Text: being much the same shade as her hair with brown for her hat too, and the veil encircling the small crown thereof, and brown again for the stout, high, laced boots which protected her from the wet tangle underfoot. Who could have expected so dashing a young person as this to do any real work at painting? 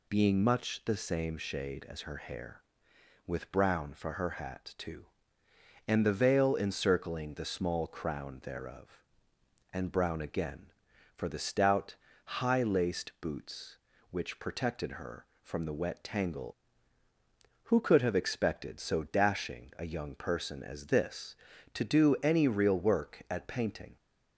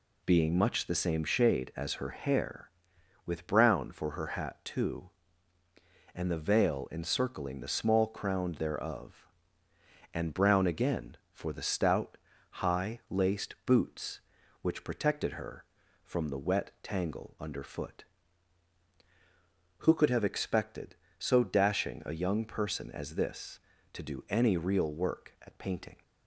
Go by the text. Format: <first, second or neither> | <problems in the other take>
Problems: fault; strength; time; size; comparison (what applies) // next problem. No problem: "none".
second | skips "underfoot"; at 17.0 s